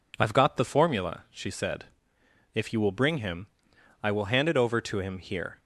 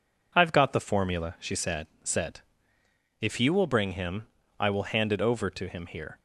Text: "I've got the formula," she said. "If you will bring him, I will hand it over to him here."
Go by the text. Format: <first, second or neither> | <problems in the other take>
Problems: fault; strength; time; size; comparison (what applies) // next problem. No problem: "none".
first | says "said" twice; at 2.0 s